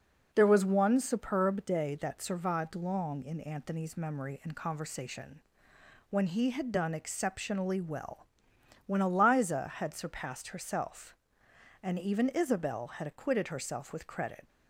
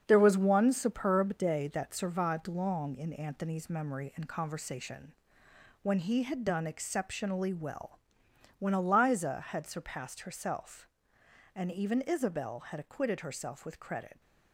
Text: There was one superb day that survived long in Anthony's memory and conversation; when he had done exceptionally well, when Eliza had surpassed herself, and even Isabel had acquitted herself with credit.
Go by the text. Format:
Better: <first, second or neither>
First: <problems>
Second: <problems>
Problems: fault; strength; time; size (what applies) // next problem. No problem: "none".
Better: first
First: none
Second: gets quieter; strong; throughout; 7.5 dB